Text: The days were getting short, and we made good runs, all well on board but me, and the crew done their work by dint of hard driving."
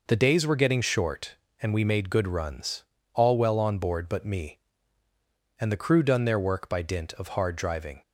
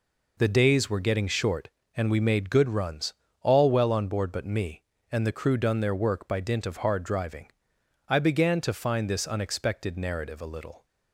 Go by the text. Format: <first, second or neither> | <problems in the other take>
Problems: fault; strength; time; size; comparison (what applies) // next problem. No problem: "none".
first | goes on to say "I began to find this unexpected narrative a little"; strong; from 8.0 s on; 2.7 s long